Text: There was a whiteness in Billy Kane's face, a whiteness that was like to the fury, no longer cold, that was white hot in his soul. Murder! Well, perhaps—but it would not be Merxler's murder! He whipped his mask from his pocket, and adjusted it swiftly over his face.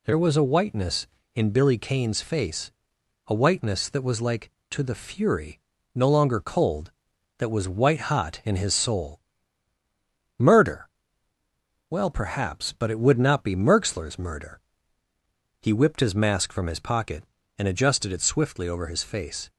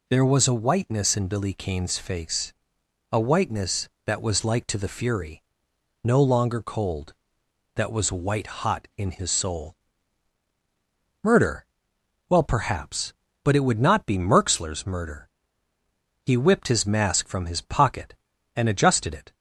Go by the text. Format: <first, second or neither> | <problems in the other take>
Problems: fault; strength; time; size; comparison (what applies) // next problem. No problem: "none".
first | stops before "swiftly over his face"; at 19.3 s